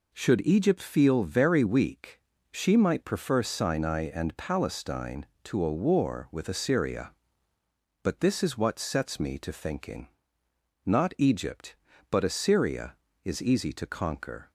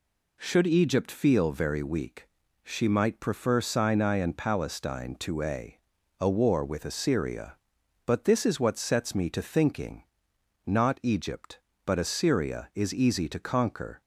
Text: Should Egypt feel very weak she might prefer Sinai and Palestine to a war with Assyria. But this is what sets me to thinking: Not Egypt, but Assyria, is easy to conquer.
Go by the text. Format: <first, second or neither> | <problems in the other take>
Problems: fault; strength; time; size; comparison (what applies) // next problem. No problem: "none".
first | pauses between "weak" and "she"; slight; at 2.2 s; 0.36 s long; slight in the first // says "a" twice; at 6.1 s